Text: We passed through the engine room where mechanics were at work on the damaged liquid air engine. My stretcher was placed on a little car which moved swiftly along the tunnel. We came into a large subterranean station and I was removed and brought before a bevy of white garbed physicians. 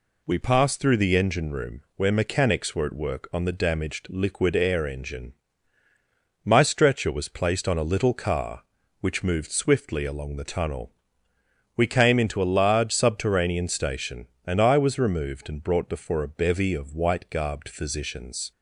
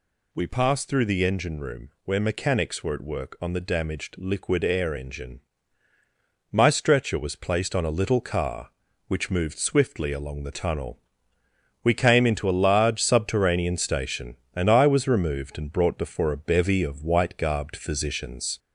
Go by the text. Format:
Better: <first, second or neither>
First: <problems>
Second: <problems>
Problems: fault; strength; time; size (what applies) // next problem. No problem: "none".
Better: first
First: pauses between "room" and "where"; slight; at 1.8 s; 0.16 s long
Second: gets louder; slight; throughout; 2 dB // pauses between "room" and "where"; slight; at 1.8 s; 0.16 s long